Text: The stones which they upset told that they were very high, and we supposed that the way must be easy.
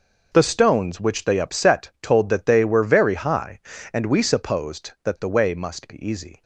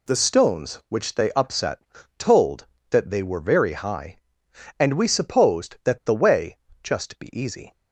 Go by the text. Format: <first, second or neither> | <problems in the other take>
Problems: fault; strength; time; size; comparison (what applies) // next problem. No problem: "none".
first | pauses between "upset" and "told"; slight; at 1.8 s; 0.36 s long // says "just" for "must"; at 6.8 s